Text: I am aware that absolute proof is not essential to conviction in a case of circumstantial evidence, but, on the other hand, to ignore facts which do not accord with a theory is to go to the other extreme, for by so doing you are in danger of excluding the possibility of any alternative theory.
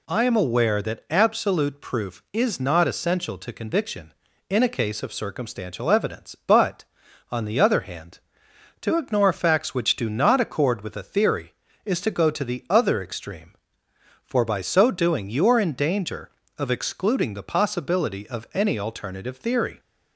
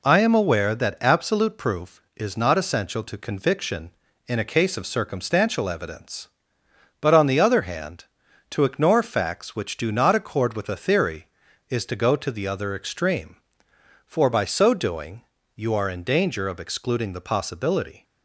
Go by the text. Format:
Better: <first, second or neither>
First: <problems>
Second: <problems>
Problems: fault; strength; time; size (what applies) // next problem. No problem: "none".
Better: first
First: none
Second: pauses between "doing" and "you"; slight; at 15.2 s; 0.34 s long // stops before "of any alternative theory"; at 18.0 s